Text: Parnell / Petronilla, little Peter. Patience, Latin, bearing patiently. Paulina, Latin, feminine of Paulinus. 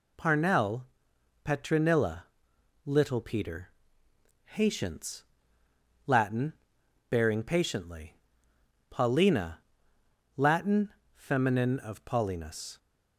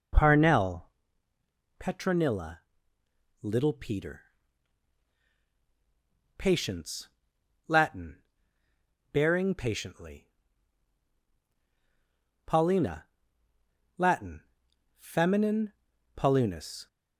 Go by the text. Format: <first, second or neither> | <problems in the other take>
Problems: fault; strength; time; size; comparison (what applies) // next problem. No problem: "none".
first | skips "of"; at 15.9 s